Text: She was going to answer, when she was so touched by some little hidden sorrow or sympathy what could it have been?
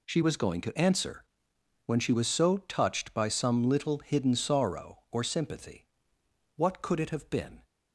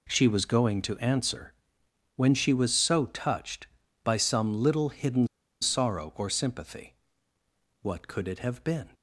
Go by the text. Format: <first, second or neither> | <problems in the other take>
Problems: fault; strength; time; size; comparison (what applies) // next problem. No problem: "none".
first | pauses between "hidden" and "sorrow"; slight; at 5.2 s; 0.34 s long // pauses between "sympathy" and "what"; noticeable; at 6.9 s; 0.86 s long; noticeable in the first